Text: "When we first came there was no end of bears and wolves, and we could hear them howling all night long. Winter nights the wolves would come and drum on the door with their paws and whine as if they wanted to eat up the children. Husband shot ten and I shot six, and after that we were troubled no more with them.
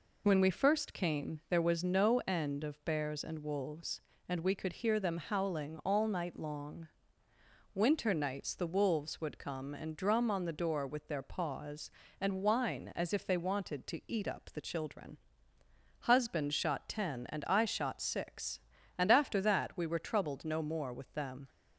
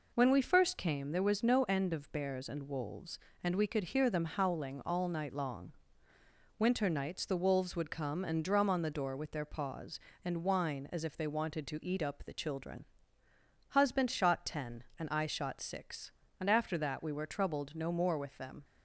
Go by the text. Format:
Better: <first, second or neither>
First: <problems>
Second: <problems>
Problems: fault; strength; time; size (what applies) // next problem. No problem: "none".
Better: neither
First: none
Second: none